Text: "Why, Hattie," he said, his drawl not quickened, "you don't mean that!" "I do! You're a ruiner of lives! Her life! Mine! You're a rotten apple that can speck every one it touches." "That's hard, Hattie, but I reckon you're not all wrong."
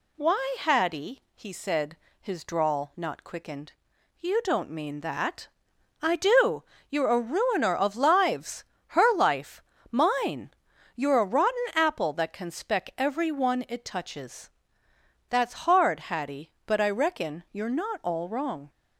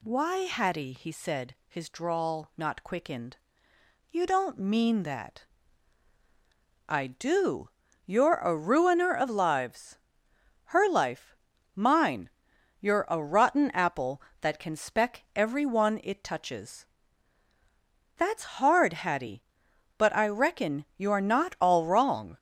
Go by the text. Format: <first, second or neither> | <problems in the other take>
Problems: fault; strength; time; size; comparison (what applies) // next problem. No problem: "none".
neither | none